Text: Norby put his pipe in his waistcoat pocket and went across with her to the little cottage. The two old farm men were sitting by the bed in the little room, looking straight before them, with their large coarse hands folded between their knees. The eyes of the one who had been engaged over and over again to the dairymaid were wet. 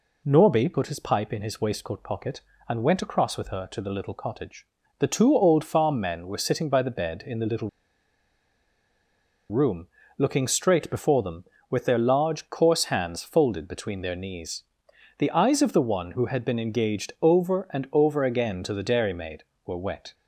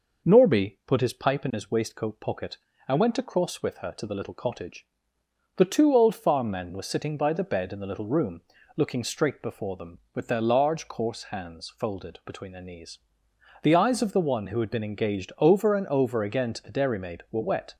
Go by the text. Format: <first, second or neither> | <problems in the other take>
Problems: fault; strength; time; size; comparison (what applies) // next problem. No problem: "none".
second | pauses between "little" and "room"; strong; at 7.6 s; 1.8 s long